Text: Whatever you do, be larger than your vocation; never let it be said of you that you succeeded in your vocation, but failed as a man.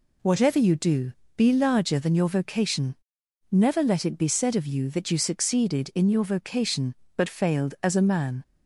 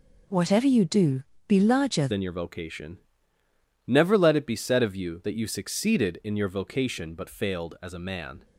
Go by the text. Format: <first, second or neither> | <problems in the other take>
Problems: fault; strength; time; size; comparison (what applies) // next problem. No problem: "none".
first | changes voice at "than"; from 2.0 s on; 6.4 s long